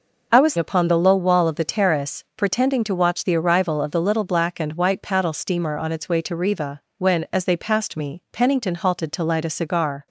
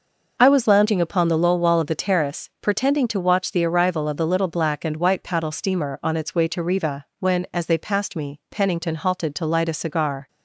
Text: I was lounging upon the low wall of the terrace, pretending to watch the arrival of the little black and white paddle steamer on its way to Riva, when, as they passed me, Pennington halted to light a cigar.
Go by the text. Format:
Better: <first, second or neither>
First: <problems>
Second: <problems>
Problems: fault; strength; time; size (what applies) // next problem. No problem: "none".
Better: second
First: skips "lounging"; at 0.5 s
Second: none